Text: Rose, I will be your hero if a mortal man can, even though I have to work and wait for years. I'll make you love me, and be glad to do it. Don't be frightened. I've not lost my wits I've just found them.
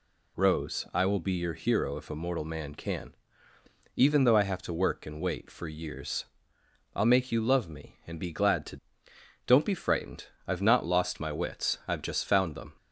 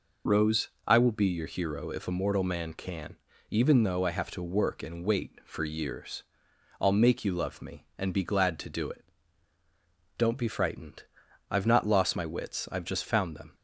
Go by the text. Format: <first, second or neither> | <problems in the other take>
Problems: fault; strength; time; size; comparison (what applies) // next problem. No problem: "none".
second | skips "do it"; at 9.1 s